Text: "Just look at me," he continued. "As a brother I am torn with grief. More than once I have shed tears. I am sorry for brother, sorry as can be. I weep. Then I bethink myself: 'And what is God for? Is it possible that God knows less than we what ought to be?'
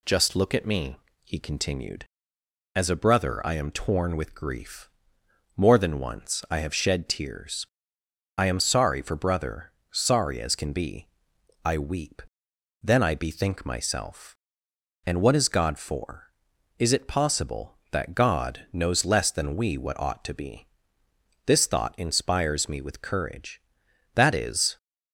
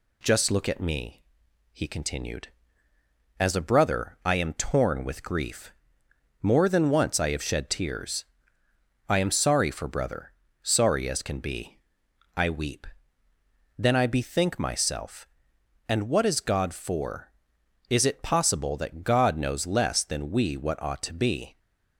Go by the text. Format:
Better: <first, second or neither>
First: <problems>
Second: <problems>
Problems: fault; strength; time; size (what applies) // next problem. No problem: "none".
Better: second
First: goes on to say "This thought inspires me with courage That is"; strong; from 21.4 s on; 3.3 s long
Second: none